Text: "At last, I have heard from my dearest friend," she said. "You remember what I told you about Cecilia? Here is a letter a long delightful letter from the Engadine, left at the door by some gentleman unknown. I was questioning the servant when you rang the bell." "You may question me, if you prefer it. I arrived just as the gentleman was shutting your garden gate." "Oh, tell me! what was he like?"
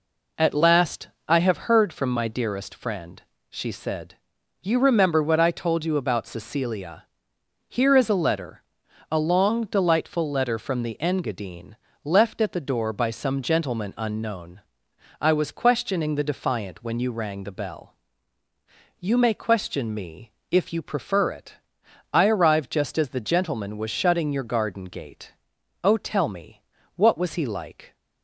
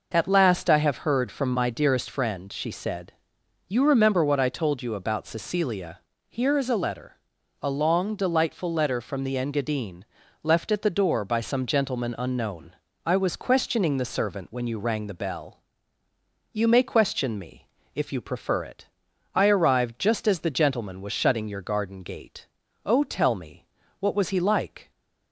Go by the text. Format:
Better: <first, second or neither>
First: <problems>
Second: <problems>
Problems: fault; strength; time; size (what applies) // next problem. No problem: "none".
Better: second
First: pauses between "letter" and "a"; noticeable; at 8.6 s; 0.50 s long // says "defiant" for "servant"; at 16.3 s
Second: pauses between "letter" and "a"; noticeable; at 7.1 s; 0.48 s long